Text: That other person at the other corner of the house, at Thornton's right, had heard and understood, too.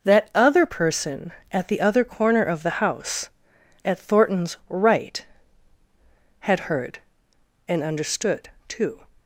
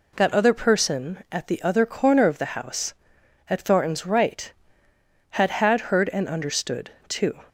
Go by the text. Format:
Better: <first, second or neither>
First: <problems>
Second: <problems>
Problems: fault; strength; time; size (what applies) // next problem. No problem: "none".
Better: first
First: none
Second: says "had" twice; at 5.5 s